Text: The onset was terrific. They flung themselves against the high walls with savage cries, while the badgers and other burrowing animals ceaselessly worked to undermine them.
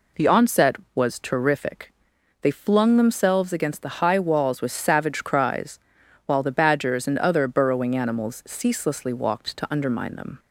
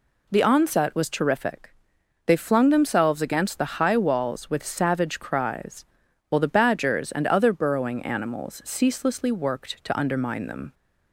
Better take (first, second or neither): second